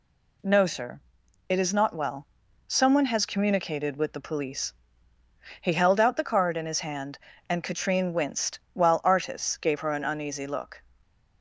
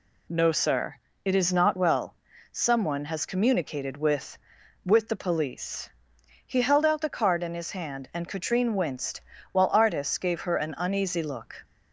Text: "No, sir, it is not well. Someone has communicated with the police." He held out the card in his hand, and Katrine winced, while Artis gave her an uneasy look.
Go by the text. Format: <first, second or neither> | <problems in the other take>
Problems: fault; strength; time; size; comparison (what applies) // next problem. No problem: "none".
first | says "with" twice; at 4.8 s